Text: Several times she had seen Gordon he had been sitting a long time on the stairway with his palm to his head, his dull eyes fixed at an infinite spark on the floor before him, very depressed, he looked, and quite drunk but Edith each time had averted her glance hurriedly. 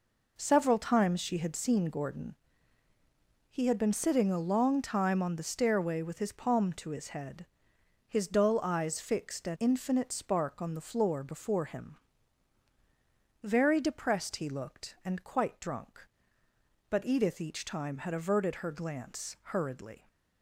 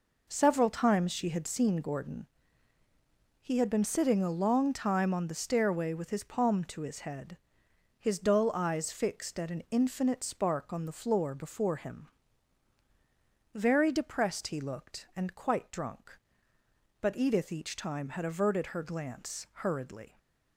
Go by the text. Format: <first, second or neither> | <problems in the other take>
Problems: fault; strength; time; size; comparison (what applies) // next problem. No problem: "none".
second | pauses between "Gordon" and "he"; at 2.3 s; 1.1 s long; also in the second // skips "an"; at 9.5 s